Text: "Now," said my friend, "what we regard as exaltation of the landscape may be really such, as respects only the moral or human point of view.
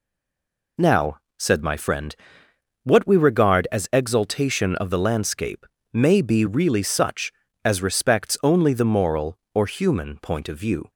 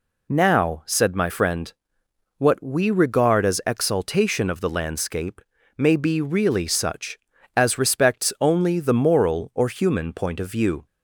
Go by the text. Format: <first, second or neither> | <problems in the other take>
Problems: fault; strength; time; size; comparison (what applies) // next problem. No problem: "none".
second | stays silent before the first word; slight; until 0.7 s; 0.7 s long // pauses between "landscape" and "may"; slight; at 5.6 s; 0.28 s long; slight in the second